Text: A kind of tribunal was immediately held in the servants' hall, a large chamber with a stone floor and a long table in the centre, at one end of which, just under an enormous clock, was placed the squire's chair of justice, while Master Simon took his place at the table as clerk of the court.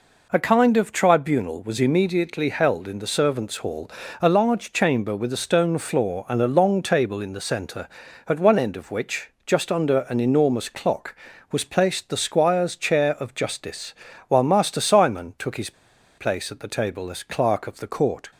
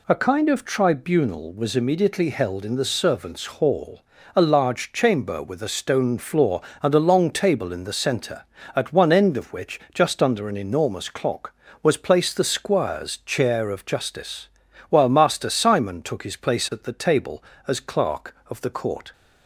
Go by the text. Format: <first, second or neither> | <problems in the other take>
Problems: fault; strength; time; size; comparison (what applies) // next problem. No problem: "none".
second | pauses between "his" and "place"; noticeable; at 15.7 s; 0.46 s long